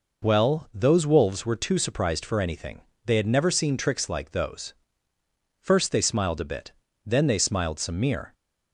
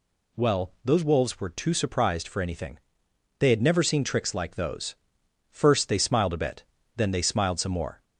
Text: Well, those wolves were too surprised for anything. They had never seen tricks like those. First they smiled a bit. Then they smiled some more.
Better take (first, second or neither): second